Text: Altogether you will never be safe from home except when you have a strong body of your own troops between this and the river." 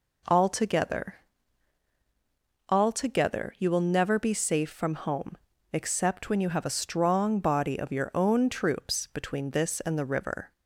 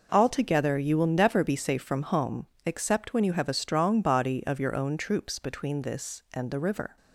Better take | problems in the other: second | says "Altogether" twice; at 2.6 s // pauses between "home" and "except"; at 5.3 s; 0.38 s long; slight in the second

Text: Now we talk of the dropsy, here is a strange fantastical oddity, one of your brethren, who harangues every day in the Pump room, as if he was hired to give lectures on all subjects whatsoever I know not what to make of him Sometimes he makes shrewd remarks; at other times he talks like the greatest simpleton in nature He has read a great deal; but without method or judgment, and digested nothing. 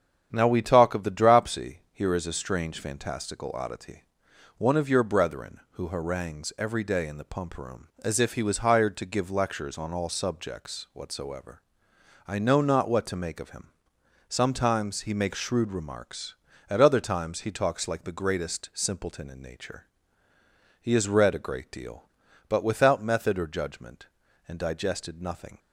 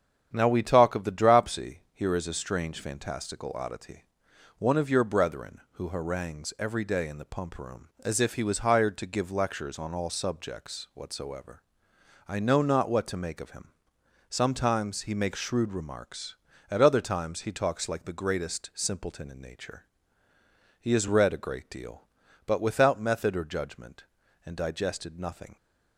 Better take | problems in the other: neither | starts louder than the rest; strong; the same in both // pauses between "whatsoever" and "I"; noticeable; the same in both // pauses between "him" and "Sometimes"; noticeable; the same in both // pauses between "nature" and "He"; noticeable; the same in both

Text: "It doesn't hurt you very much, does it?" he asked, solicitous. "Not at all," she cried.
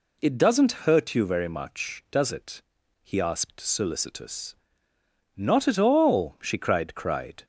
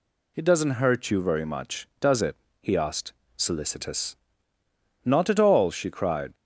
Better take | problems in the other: second | says "cried" twice; at 6.9 s

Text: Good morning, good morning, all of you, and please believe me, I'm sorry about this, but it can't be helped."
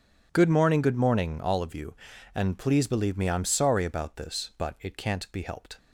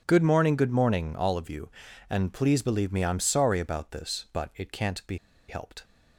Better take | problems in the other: first | pauses between "be" and "helped"; slight; at 5.1 s; 0.33 s long

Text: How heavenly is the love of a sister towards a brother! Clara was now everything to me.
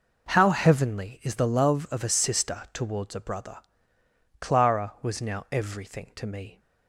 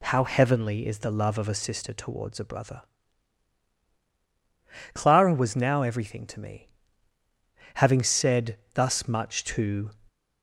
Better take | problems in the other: first | goes on to say "Having said thus much to"; strong; from 7.7 s on; 2.1 s long

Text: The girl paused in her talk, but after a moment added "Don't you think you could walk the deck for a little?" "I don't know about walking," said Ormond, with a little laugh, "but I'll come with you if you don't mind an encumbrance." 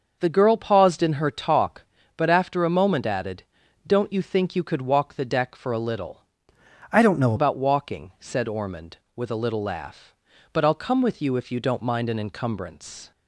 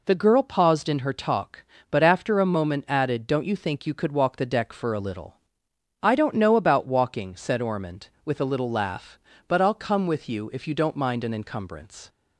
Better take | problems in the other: second | pauses between "added" and "Don't"; at 3.4 s; 0.42 s long // changes voice from "I" to "know"; from 6.9 to 7.3 s; 0.4 s long

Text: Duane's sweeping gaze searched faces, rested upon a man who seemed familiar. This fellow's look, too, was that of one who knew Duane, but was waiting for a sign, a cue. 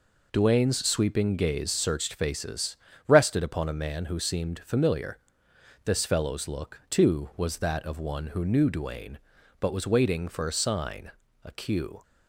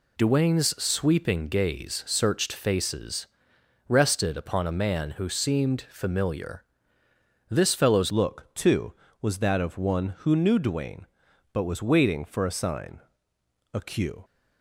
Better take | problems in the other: first | changes voice at "look"; from 8.1 s on; 6.1 s long

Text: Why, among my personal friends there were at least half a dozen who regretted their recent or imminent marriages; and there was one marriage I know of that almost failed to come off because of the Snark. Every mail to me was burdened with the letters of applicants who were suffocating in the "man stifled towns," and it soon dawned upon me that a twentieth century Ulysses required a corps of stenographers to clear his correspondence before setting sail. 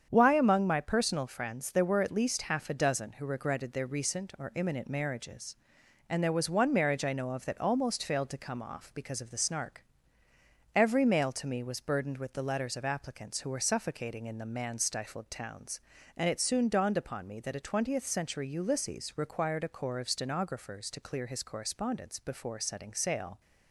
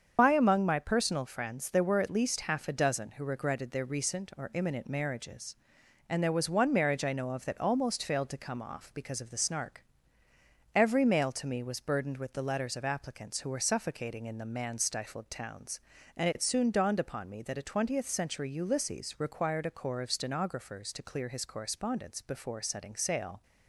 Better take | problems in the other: first | loses the start of "Why"; at 0.1 s; 100 ms // starts louder than the rest; strong; until 1.1 s; 7 dB; strong in the first

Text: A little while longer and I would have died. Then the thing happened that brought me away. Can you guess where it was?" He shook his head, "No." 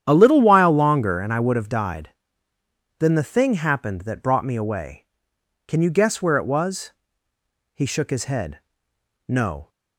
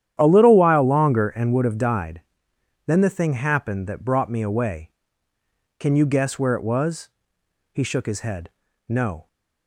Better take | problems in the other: first | starts louder than the rest; strong; until 1.2 s; 10.5 dB; strong in the first // skips "I"; at 1.5 s

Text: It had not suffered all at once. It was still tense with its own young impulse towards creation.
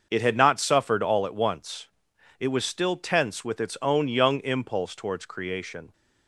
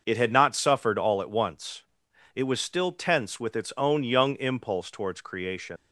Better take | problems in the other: first | starts louder than the rest; noticeable; until 1.0 s; 6 dB; also in the first // leaves "creation" unfinished; at 5.7 s; 115 ms

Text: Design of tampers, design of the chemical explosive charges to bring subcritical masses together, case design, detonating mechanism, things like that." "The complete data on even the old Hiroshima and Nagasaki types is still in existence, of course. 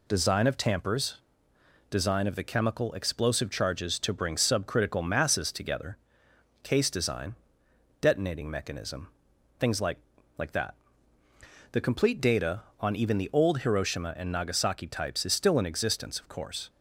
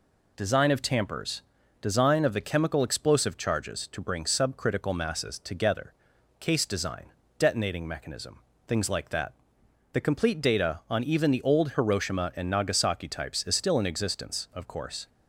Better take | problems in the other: second | says "like" twice; at 10.3 s

